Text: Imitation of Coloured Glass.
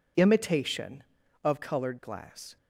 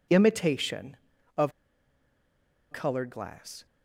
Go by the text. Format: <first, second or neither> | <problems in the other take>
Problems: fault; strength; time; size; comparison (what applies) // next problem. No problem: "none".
first | pauses between "of" and "Coloured"; at 1.5 s; 1.1 s long